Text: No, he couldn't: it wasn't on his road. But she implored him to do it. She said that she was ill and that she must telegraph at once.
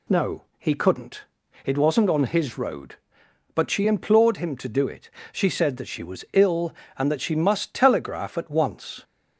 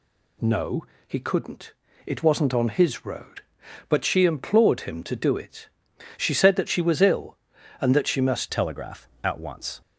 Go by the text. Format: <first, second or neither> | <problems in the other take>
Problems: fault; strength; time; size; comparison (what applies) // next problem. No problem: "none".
first | changes voice at "telegraph"; from 8.5 s on; 1.3 s long